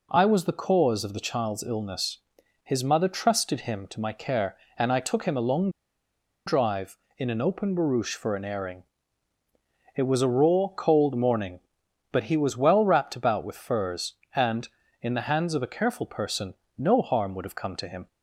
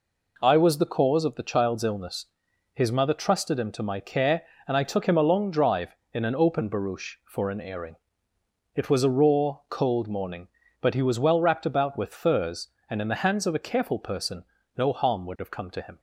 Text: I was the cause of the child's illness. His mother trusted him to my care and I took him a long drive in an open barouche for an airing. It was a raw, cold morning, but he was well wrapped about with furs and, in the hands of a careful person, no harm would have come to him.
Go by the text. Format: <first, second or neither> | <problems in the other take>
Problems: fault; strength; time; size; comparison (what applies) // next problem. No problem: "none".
second | pauses between "long" and "drive"; noticeable; at 5.6 s; 0.77 s long